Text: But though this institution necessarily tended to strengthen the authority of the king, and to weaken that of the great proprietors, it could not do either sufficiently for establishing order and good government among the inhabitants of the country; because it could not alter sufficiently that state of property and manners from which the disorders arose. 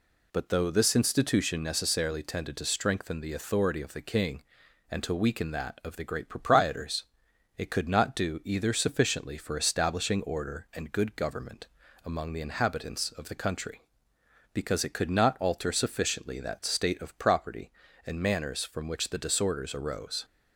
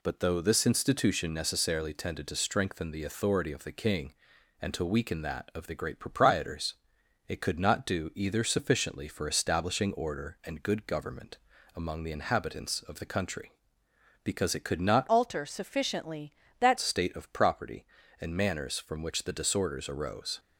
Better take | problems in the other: first | pauses between "government" and "among"; at 11.3 s; 0.40 s long; also in the first // changes voice from "alter" to "that"; from 15.0 to 16.7 s; 1.7 s long

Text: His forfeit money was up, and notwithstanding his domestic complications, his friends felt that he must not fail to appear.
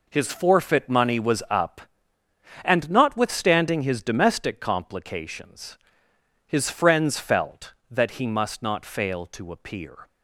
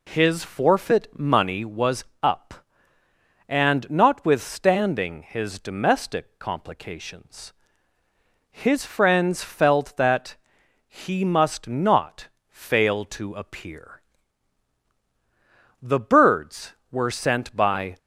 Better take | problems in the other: first | pauses between "was" and "up"; slight; at 2.0 s; 0.18 s long // pauses between "that" and "he"; noticeable; at 10.3 s; 0.52 s long // pauses between "not" and "fail"; slight; at 12.2 s; 0.22 s long // goes on to say "The birds were sent by"; strong; from 15.8 s on; 2.1 s long

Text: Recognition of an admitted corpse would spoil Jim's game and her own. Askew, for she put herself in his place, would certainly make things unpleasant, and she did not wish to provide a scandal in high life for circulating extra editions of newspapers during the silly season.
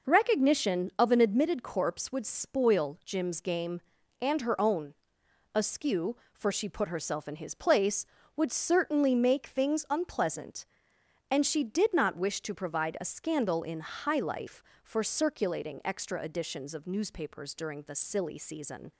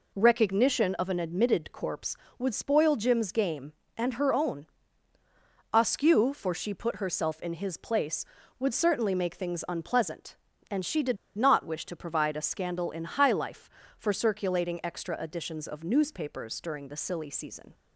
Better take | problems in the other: first | pauses between "did" and "not"; slight; at 11.1 s; 0.21 s long

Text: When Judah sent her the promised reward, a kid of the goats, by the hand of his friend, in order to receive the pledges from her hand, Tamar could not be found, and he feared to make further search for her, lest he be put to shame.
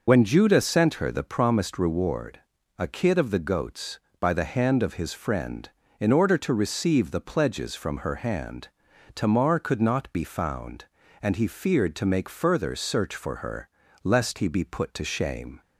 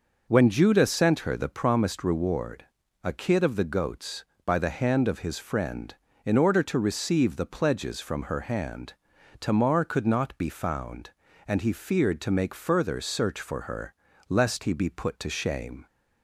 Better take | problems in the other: second | loses the start of "When"; at 0.0 s; 35 ms

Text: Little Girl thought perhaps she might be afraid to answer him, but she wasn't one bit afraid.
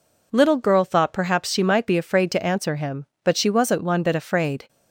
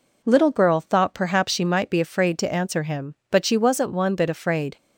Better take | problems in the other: neither | none

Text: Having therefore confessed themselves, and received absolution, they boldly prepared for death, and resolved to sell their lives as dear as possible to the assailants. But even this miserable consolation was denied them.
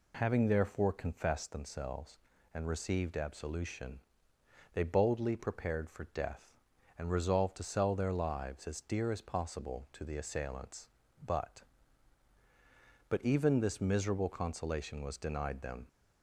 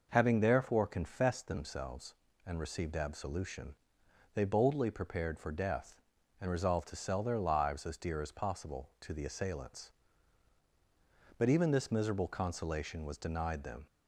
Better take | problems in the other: second | says "But" twice; at 13.0 s

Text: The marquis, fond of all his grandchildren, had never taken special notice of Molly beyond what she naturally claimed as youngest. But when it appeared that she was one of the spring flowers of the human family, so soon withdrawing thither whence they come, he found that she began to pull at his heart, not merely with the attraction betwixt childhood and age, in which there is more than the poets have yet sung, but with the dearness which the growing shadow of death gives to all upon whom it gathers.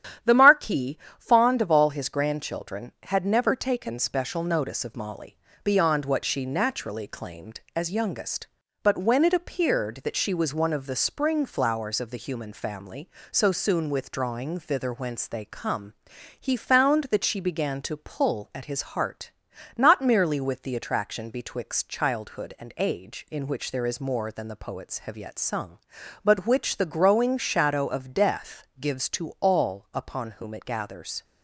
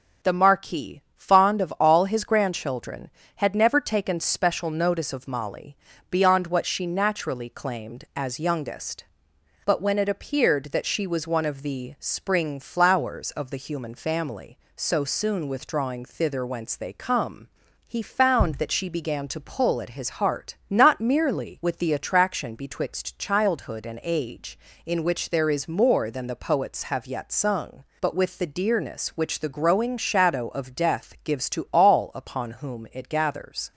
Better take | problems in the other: second | starts louder than the rest; strong; until 1.4 s; 10 dB; also in the second // pauses between "Molly" and "beyond"; slight; at 5.3 s; 0.26 s long; slight in the second // skips "with the dearness"; at 26.4 s

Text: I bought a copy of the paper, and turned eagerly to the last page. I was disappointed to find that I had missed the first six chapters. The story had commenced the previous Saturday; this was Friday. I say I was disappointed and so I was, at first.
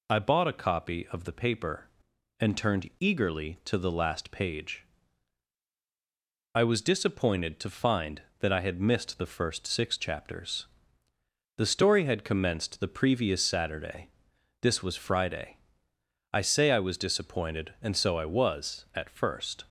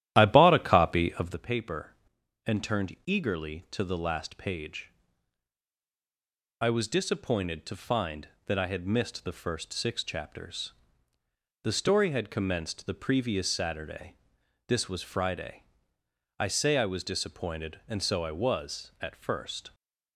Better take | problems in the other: first | starts louder than the rest; strong; until 1.5 s; 12.5 dB

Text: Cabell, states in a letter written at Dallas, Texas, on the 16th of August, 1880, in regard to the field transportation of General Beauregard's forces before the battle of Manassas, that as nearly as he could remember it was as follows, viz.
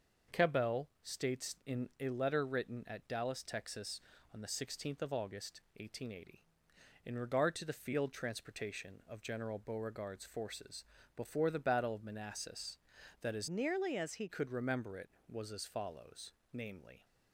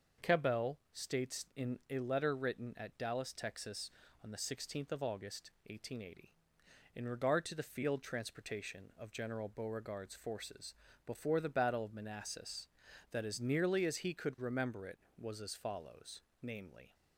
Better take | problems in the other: second | starts louder than the rest; noticeable; until 1.4 s; 6 dB; noticeable in the second // pauses between "forces" and "before"; slight; at 10.8 s; 0.32 s long; slight in the second // changes voice from "nearly" to "he"; from 13.4 to 14.2 s; 0.8 s long

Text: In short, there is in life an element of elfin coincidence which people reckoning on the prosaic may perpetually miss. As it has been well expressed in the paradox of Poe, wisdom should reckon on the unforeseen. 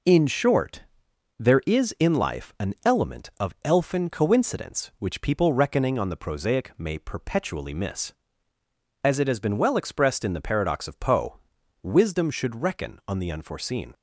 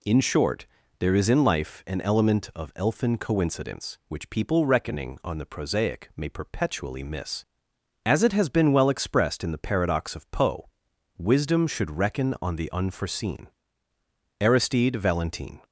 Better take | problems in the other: first | goes on to say "Aristide Valentin"; noticeable; from 14.4 s on; 1.2 s long

